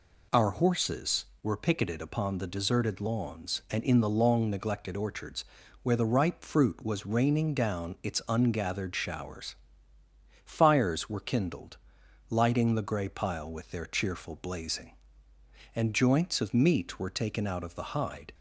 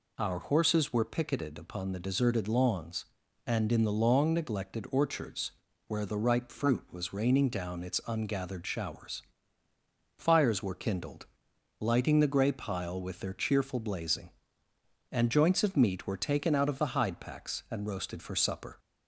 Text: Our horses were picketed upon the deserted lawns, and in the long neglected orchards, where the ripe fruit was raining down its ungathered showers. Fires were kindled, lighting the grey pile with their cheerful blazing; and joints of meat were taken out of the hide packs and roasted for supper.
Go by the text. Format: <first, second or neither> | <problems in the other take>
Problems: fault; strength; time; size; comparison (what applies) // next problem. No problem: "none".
second | stops before "packs and roasted for supper"; at 18.3 s